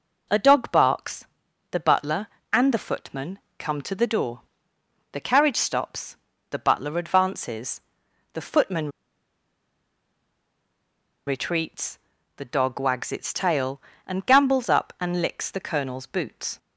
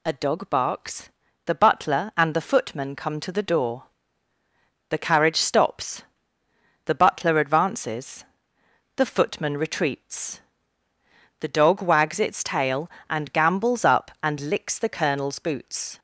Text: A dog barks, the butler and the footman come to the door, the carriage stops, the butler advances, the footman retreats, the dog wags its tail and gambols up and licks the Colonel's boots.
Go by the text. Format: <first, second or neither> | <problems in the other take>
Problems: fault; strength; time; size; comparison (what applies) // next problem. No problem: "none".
second | pauses between "footman" and "come"; slight; at 3.3 s; 0.20 s long // pauses between "footman" and "retreats"; strong; at 8.8 s; 2.3 s long